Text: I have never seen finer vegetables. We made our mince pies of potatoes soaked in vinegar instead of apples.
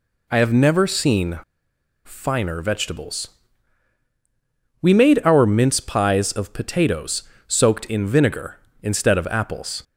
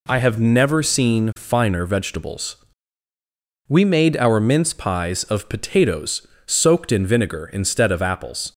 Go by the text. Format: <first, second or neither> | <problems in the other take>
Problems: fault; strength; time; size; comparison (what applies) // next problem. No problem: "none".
second | pauses between "seen" and "finer"; noticeable; at 1.3 s; 0.65 s long // pauses between "potatoes" and "soaked"; slight; at 7.2 s; 0.24 s long; slight in the second